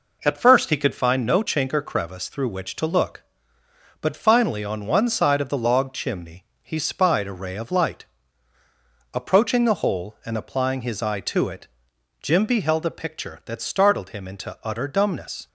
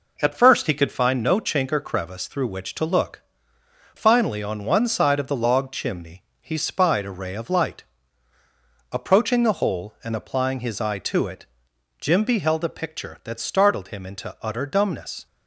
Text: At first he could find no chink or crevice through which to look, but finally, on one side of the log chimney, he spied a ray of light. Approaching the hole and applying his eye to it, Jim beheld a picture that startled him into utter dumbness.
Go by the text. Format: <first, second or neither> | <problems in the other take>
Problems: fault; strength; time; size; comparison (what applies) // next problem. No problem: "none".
first | skips "but"; at 3.5 s